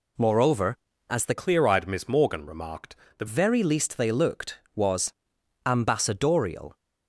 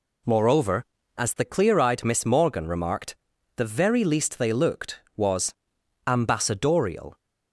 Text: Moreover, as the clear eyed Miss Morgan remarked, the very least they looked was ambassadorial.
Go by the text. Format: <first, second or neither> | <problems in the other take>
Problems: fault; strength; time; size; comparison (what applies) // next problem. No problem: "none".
second | changes voice from "clear" to "the"; from 1.3 to 3.2 s; 1.9 s long // pauses between "was" and "ambassadorial"; noticeable; at 5.1 s; 0.54 s long; noticeable in the second